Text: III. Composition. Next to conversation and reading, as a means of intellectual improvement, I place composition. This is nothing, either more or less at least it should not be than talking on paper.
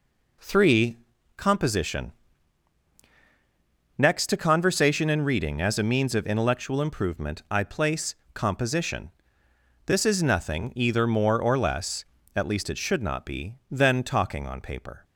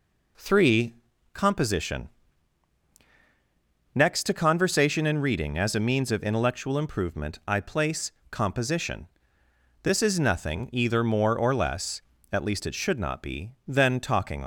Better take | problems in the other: first | pauses between "place" and "composition"; slight; at 8.1 s; 0.18 s long; slight in the first // stops before "on paper"; at 14.4 s

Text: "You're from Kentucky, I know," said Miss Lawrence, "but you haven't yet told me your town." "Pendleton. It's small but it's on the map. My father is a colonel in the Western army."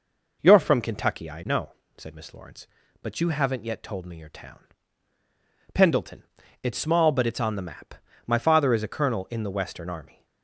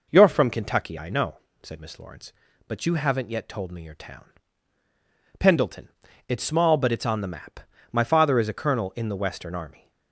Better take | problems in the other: neither | none

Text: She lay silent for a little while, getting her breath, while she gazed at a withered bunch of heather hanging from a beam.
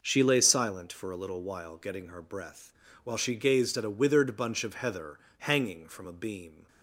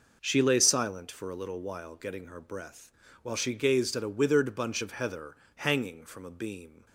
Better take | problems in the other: neither | pauses between "heather" and "hanging"; slight; the same in both

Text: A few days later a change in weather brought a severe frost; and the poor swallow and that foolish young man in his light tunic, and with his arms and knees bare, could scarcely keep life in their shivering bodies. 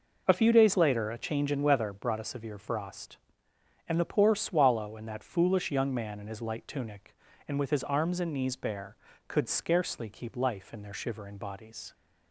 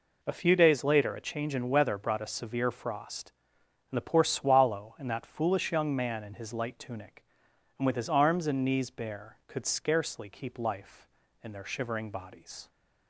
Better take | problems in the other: neither | none

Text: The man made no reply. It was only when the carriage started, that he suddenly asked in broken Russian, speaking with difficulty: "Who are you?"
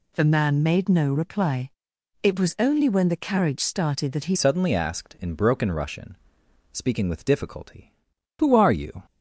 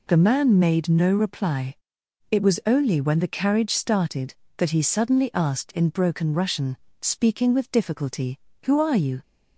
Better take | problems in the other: second | changes voice at "suddenly"; from 4.3 s on; 4.7 s long

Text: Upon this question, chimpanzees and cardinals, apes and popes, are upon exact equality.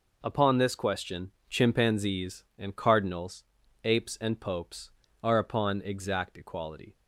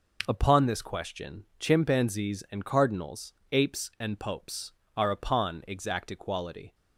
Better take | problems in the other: neither | none

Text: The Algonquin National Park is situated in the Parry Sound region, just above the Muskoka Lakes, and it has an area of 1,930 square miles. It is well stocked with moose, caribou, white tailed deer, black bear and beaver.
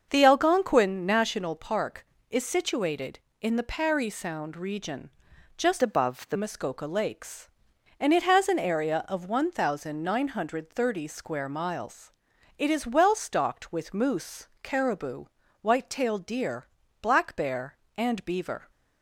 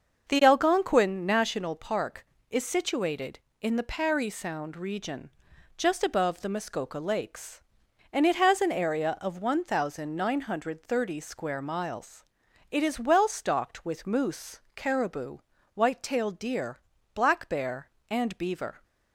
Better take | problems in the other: second | starts louder than the rest; until 1.1 s; 6.5 dB // changes voice from "above" to "the"; from 5.8 to 6.3 s; 0.5 s long

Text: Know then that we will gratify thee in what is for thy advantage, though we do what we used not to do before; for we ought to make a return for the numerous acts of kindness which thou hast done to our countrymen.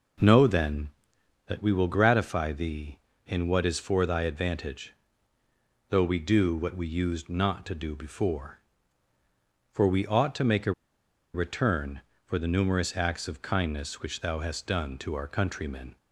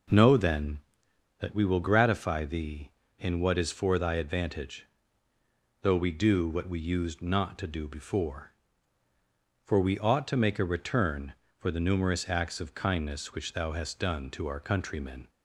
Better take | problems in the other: second | pauses between "a" and "return"; noticeable; at 10.7 s; 0.61 s long

